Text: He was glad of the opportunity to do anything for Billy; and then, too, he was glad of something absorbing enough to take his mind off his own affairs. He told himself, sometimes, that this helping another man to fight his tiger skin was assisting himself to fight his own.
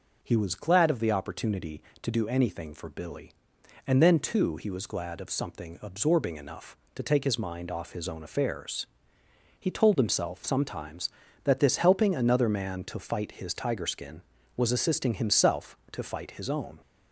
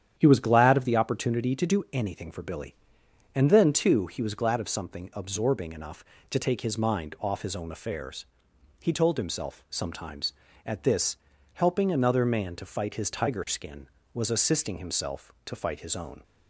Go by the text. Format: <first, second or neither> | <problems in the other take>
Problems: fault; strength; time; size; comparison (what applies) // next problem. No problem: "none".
first | starts louder than the rest; strong; until 1.1 s; 9.5 dB // says "at" for "that"; at 10.6 s // pauses between "this" and "helping"; slight; at 11.1 s; 0.36 s long